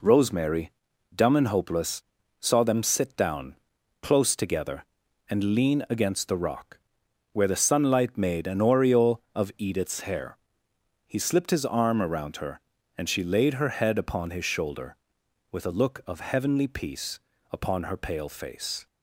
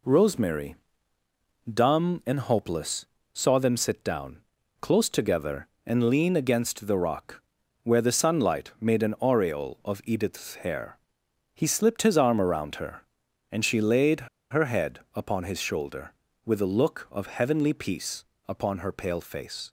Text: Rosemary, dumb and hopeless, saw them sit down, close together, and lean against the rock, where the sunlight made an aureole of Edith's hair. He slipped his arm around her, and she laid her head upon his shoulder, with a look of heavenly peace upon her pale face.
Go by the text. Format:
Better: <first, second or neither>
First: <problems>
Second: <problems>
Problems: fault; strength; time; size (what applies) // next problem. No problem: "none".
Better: first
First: pauses between "peace" and "upon"; slight; at 17.1 s; 0.32 s long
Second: pauses between "laid" and "her"; slight; at 14.2 s; 0.22 s long // pauses between "head" and "upon"; slight; at 14.9 s; 0.16 s long // pauses between "peace" and "upon"; slight; at 18.2 s; 0.24 s long